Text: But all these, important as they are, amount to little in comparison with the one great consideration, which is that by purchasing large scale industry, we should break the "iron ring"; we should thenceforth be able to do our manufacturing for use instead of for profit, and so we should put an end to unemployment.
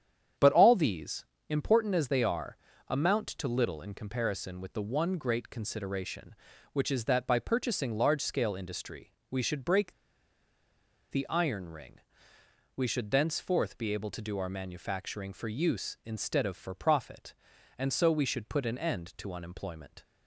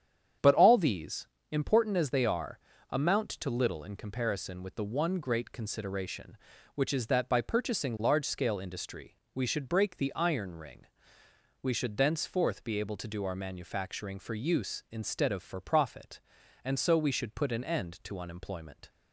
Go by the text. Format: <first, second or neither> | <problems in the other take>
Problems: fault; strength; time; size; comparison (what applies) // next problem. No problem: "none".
second | starts louder than the rest; strong; until 1.6 s; 9 dB; strong in the second // pauses between "break" and "the"; at 9.9 s; 1.1 s long